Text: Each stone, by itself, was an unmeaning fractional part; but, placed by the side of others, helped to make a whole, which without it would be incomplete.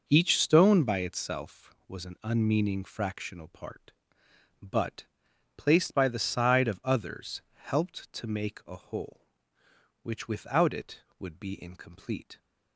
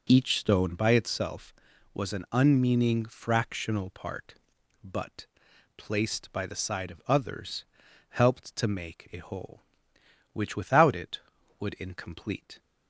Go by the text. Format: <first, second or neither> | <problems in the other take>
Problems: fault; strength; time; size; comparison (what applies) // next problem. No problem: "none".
first | starts louder than the rest; noticeable; until 1.0 s; 6 dB // skips "be"; at 11.7 s